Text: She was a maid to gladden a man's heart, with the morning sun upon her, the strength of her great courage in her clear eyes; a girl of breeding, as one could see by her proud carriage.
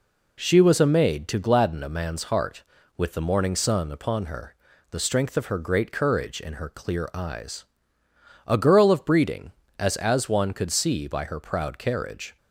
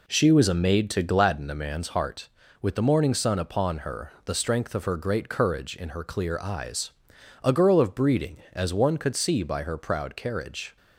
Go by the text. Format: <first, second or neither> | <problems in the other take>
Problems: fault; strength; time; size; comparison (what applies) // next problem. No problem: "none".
second | says "as" twice; at 9.9 s